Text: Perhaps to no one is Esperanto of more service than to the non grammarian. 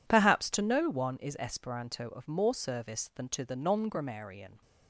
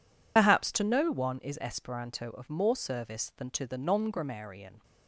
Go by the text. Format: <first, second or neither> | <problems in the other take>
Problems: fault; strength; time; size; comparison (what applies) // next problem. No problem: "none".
first | loses the start of "Perhaps"; at 0.3 s; 60 ms